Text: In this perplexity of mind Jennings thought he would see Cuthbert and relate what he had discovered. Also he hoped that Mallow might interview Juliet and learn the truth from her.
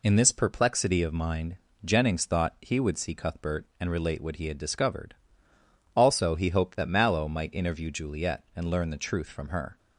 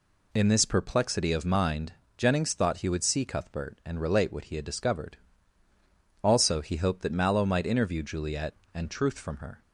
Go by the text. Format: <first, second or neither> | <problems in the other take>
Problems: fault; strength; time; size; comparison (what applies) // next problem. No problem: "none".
first | pauses between "mind" and "Jennings"; slight; at 1.9 s; 0.24 s long; slight in the first // skips "learn the"; at 8.8 s